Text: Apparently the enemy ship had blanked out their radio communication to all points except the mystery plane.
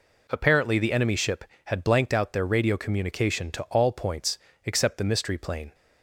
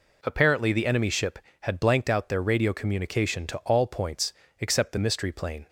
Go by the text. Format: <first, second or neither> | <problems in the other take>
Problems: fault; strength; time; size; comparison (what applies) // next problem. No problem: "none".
neither | pauses between "points" and "except"; slight; the same in both